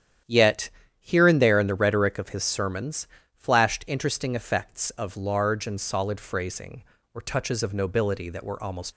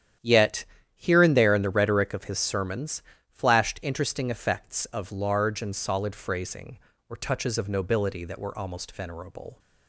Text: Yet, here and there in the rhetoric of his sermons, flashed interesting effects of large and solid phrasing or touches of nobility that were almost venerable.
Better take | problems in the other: second | starts louder than the rest; strong; until 1.5 s; 10 dB; strong in the second // stops before "venerable"; at 8.9 s

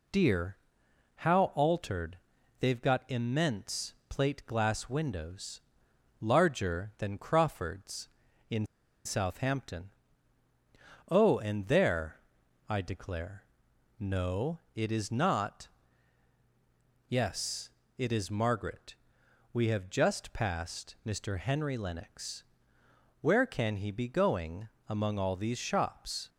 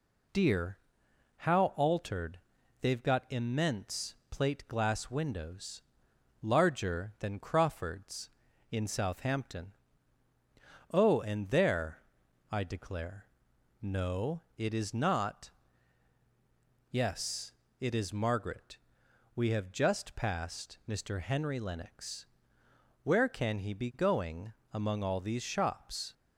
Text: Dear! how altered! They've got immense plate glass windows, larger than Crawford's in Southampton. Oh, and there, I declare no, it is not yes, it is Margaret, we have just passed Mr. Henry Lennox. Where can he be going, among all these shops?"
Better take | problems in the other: second | pauses between "immense" and "plate"; slight; at 3.9 s; 0.16 s long; slight in the second // pauses between "in" and "Southampton"; at 8.6 s; 0.39 s long // pauses between "declare" and "no"; noticeable; at 13.4 s; 0.56 s long; noticeable in the second // pauses between "not" and "yes"; strong; at 15.6 s; 1.4 s long; strong in the second

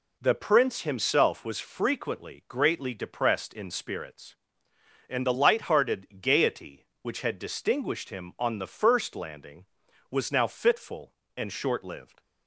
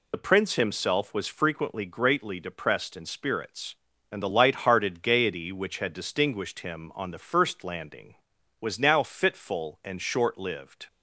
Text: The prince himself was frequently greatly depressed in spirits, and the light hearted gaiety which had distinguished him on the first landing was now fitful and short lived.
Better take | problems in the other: first | loses the start of "The"; at 0.1 s; 40 ms

